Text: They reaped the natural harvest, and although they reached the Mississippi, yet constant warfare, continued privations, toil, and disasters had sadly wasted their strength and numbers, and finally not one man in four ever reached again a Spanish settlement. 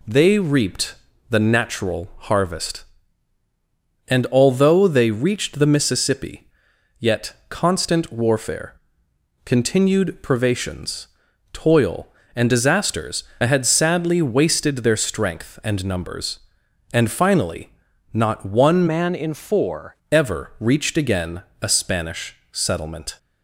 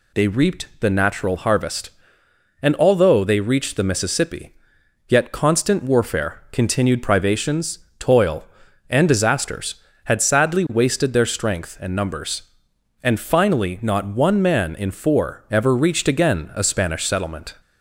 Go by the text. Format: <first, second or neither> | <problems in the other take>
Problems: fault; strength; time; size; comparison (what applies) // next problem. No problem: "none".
second | pauses between "reaped" and "the"; slight; at 0.9 s; 0.34 s long // pauses between "yet" and "constant"; slight; at 7.3 s; 0.16 s long // pauses between "finally" and "not"; at 17.6 s; 0.42 s long // changes voice from "man" to "four"; from 18.8 to 19.9 s; 1.1 s long // pauses between "again" and "a"; slight; at 21.4 s; 0.20 s long // pauses between "Spanish" and "settlement"; slight; at 22.3 s; 0.16 s long